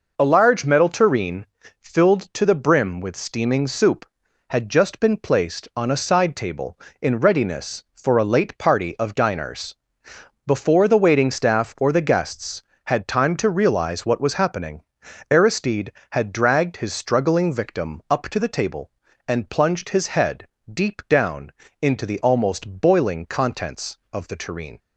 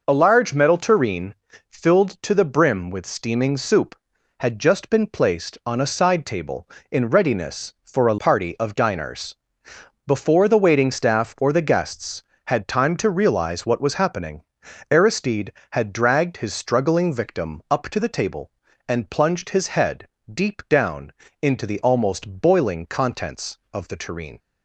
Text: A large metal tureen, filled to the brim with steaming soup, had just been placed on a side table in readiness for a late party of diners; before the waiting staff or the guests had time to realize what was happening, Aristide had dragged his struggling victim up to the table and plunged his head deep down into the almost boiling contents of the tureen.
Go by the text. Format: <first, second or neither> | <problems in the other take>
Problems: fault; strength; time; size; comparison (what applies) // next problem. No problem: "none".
first | skips "late"; at 8.1 s // pauses between "head" and "deep"; slight; at 20.0 s; 0.26 s long; slight in the first // pauses between "down" and "into"; slight; at 21.1 s; 0.32 s long; slight in the first